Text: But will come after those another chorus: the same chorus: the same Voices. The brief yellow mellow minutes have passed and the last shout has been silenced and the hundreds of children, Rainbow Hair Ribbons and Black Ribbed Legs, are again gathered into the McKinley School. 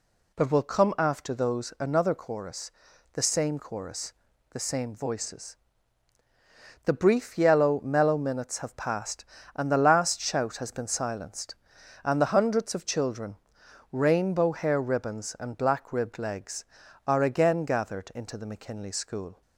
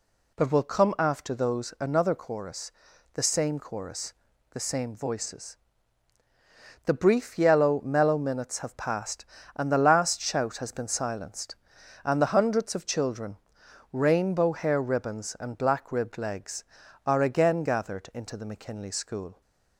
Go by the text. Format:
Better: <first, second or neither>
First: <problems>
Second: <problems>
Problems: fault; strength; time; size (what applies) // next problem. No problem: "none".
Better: neither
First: none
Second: none